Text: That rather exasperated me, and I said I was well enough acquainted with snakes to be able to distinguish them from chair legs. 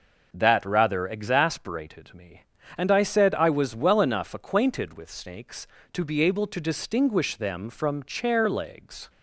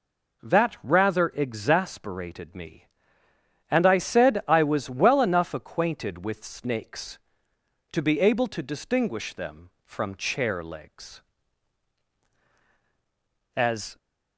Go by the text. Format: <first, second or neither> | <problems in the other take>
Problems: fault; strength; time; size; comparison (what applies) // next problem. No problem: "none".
first | goes on to say "As"; slight; from 13.5 s on; 0.42 s long